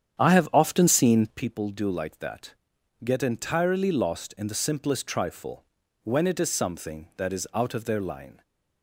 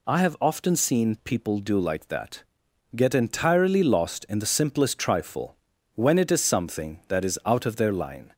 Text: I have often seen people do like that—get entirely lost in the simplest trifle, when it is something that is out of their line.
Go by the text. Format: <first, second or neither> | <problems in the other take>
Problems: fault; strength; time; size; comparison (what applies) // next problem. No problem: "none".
second | starts louder than the rest; strong; until 1.4 s; 9 dB